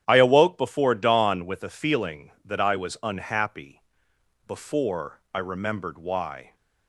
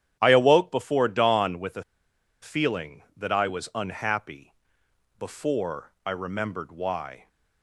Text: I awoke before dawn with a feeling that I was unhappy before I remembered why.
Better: first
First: starts louder than the rest; strong; until 1.0 s; 10.5 dB // pauses between "unhappy" and "before"; noticeable; at 3.8 s; 0.66 s long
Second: starts louder than the rest; strong; until 1.2 s; 10.5 dB // pauses between "a" and "feeling"; noticeable; at 1.8 s; 0.58 s long // pauses between "unhappy" and "before"; noticeable; at 4.5 s; 0.66 s long

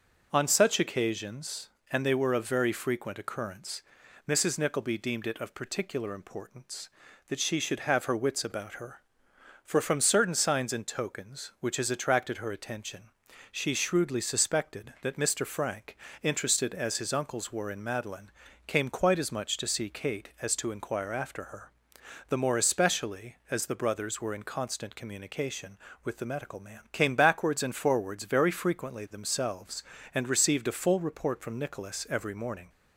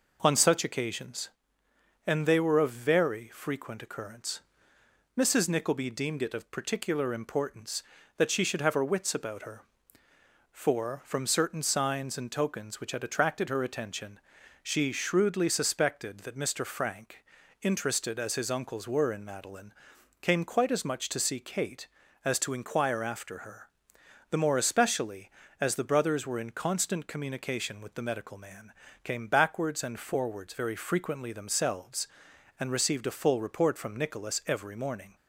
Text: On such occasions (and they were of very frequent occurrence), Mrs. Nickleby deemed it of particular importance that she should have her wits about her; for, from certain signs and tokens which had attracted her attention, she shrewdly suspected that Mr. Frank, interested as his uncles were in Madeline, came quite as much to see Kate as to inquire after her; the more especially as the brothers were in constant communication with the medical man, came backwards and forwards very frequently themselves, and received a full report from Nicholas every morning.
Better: second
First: says "has" for "had"; at 11.7 s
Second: none

